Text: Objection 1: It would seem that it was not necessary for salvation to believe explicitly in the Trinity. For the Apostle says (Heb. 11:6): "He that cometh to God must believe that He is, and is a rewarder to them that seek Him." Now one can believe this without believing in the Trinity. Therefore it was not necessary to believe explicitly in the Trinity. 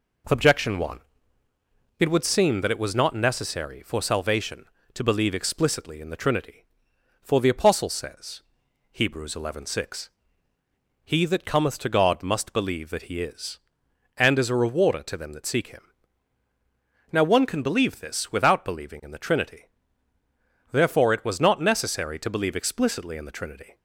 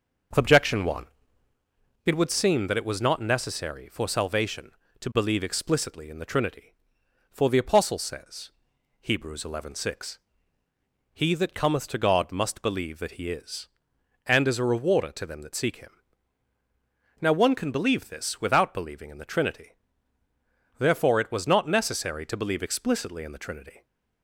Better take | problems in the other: first | starts louder than the rest; noticeable; until 1.7 s; 6 dB

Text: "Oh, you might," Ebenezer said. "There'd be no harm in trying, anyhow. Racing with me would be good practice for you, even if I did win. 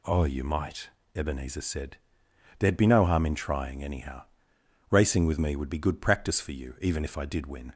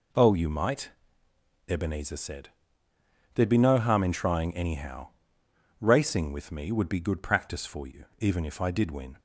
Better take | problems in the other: neither | none

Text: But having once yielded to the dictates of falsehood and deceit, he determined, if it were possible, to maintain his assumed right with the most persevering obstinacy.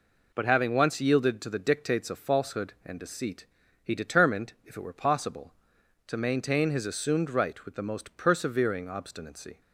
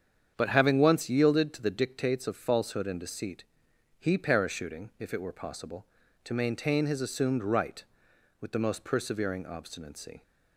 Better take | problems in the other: first | starts louder than the rest; strong; until 1.3 s; 8 dB // says "parachuting" for "determined"; at 4.1 s

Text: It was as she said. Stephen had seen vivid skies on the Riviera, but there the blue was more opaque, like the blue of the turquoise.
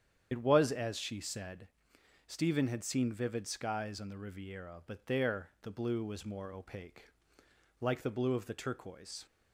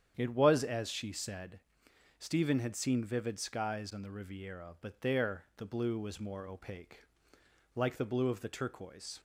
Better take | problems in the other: second | loses the start of "It"; at 0.3 s; 75 ms // starts louder than the rest; strong; until 1.3 s; 8.5 dB; strong in the second

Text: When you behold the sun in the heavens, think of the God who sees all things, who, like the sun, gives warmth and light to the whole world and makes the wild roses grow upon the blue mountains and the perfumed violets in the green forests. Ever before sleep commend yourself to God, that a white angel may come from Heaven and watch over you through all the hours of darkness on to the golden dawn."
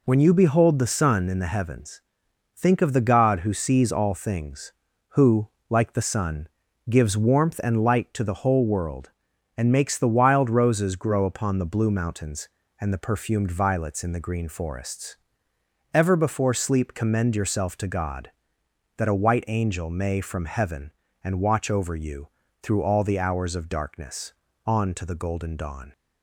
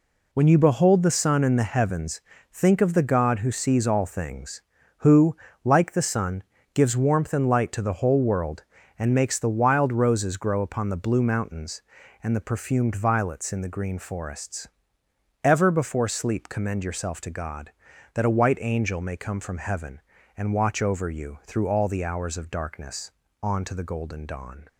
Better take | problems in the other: second | skips "come"; at 20.1 s // pauses between "you" and "through"; at 22.2 s; 0.36 s long

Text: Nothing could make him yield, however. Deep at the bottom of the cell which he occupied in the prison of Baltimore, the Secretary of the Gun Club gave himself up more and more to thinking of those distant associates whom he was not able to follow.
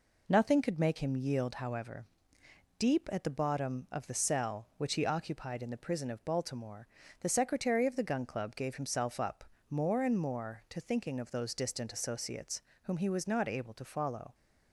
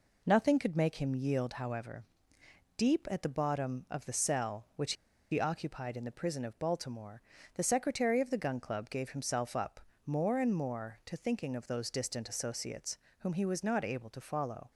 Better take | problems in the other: first | pauses between "which" and "he"; at 4.9 s; 0.38 s long // pauses between "up" and "more"; slight; at 9.8 s; 0.24 s long; slight in the first // pauses between "associates" and "whom"; slight; at 12.9 s; 0.22 s long; slight in the first

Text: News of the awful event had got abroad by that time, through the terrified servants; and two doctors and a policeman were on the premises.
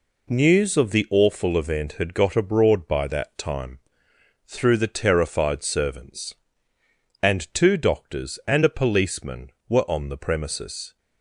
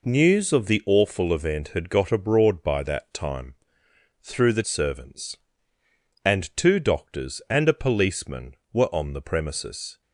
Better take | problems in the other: first | skips "terrified"; at 4.6 s

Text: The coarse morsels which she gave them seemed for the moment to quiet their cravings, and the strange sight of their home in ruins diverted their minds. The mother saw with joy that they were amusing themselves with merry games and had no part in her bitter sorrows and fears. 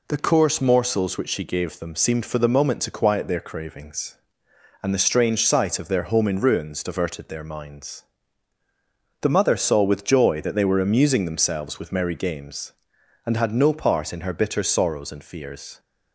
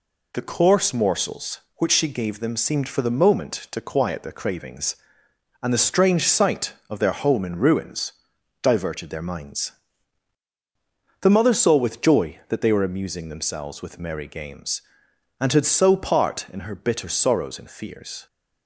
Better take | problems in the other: first | pauses between "ruins" and "diverted"; noticeable; at 8.1 s; 0.50 s long // says "so" for "no"; at 15.6 s

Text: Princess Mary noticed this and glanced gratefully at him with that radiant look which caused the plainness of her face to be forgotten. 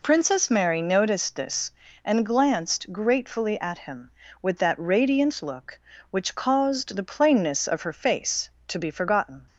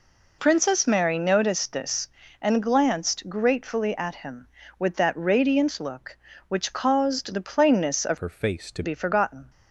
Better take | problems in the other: first | changes voice from "her" to "to"; from 8.1 to 8.8 s; 0.7 s long

